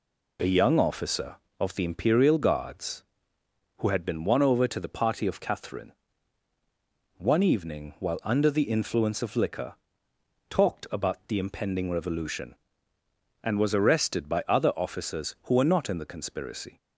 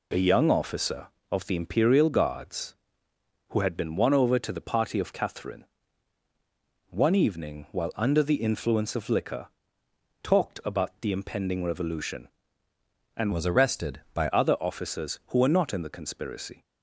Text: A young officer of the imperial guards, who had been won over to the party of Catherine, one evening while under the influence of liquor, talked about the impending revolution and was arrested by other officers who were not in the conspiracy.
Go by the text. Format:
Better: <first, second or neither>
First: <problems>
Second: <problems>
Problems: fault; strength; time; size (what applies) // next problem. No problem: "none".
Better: first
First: none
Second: changes voice from "was" to "by"; from 13.3 to 14.2 s; 0.9 s long